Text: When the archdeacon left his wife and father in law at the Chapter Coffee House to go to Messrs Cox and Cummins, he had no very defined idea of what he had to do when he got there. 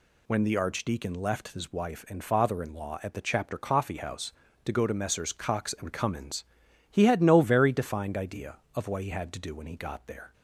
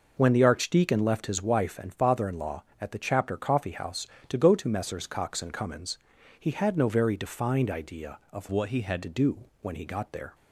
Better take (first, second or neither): first